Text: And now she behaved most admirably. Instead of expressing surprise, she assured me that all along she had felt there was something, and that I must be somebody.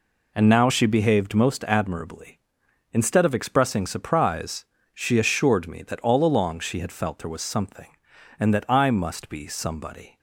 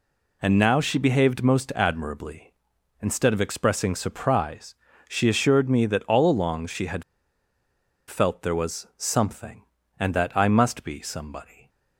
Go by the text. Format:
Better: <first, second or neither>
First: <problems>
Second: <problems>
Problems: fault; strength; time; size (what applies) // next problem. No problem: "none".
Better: first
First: none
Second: pauses between "had" and "felt"; at 7.0 s; 1.0 s long